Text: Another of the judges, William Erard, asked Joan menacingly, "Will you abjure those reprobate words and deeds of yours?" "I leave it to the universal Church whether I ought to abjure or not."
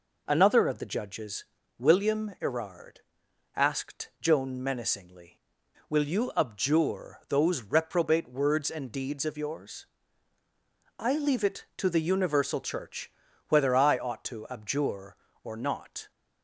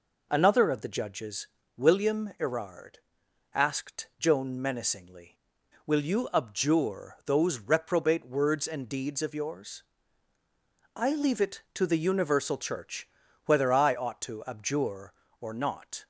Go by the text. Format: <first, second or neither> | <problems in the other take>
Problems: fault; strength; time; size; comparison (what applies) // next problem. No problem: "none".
neither | pauses between "Church" and "whether"; the same in both